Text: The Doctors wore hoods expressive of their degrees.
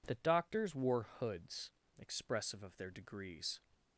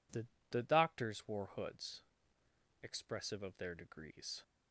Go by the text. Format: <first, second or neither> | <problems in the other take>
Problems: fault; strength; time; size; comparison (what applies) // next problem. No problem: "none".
first | says "The" twice; at 0.5 s // pauses between "hoods" and "expressive"; noticeable; at 2.0 s; 0.80 s long; slight in the first